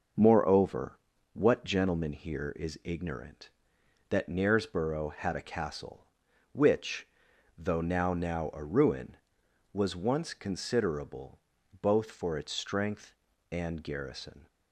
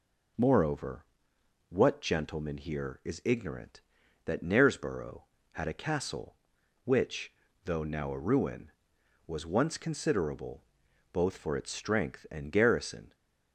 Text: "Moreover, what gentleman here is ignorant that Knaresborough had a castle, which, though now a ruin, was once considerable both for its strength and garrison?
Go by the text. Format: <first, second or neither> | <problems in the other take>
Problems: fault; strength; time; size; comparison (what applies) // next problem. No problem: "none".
second | says "now" twice; at 8.1 s // pauses between "considerable" and "both"; at 11.3 s; 0.42 s long; noticeable in the second